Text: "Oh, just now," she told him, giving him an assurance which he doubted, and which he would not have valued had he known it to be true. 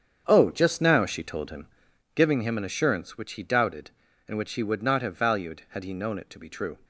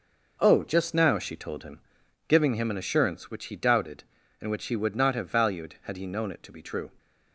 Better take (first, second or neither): second